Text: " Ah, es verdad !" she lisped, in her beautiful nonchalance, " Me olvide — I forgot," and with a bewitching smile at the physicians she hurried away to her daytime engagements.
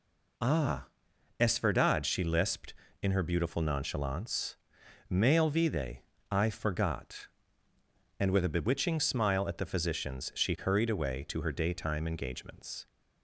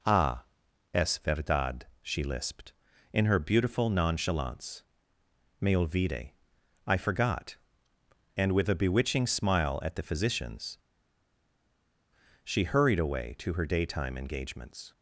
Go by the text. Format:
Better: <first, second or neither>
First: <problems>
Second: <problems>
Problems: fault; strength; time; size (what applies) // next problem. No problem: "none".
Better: first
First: none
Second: pauses between "physicians" and "she"; strong; at 10.7 s; 1.6 s long